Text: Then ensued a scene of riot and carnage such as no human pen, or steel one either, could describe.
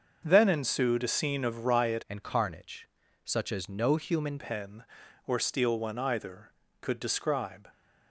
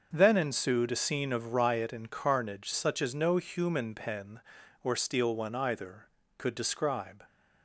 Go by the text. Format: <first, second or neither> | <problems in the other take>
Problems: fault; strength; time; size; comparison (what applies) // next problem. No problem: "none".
second | starts louder than the rest; until 1.2 s; 6.5 dB; also in the second // changes voice from "and" to "human"; from 2.0 to 4.3 s; 2.3 s long // pauses between "carnage" and "such"; at 2.8 s; 0.40 s long